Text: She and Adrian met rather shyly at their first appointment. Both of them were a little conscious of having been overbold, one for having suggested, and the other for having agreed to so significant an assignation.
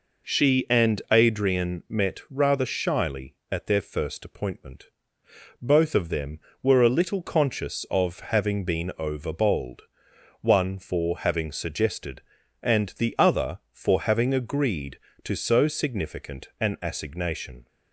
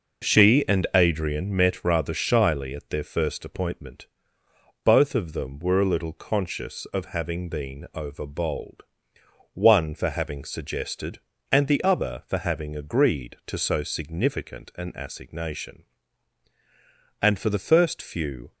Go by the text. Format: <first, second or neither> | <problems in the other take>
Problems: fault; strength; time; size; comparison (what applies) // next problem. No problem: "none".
first | goes on to say "And for the first few"; from 17.2 s on; 1.3 s long